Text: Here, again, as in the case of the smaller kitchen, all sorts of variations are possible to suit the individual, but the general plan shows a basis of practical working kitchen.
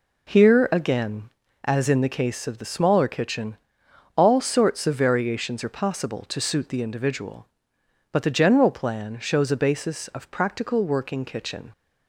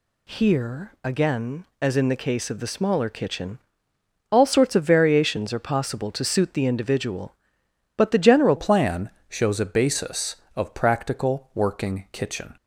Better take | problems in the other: first | changes voice at "plan"; from 8.5 s on; 4.0 s long // pauses between "plan" and "shows"; slight; at 9.0 s; 0.18 s long

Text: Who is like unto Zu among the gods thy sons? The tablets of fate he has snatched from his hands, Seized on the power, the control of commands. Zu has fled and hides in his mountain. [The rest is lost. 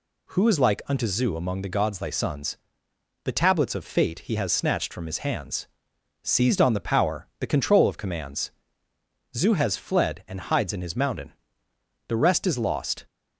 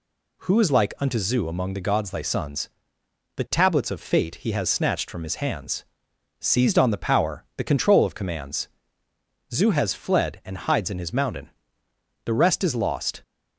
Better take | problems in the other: neither | none

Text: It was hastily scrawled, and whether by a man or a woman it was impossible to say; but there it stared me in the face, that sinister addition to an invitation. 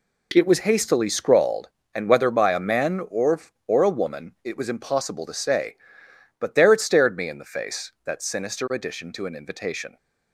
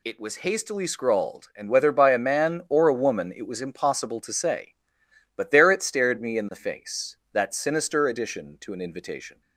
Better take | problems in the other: second | says "or" twice; at 3.6 s

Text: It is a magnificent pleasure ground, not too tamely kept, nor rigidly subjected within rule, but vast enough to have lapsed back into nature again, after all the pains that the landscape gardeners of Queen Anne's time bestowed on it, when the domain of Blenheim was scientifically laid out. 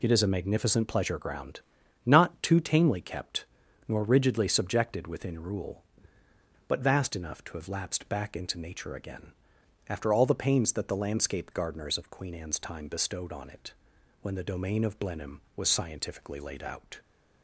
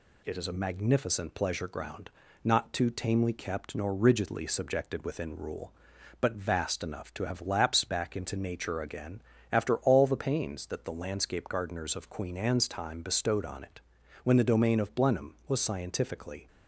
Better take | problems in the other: first | stops before "laid out"; at 16.4 s

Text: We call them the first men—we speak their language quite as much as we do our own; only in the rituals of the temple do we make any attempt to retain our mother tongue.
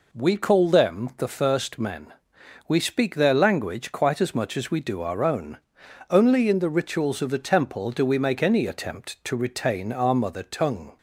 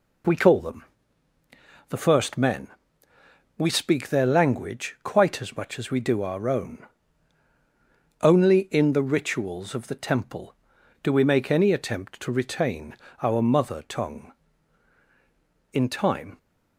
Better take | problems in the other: first | pauses between "them" and "the"; at 0.8 s; 1.0 s long // pauses between "retain" and "our"; slight; at 12.9 s; 0.26 s long // goes on to say "In time"; noticeable; from 15.7 s on; 0.66 s long

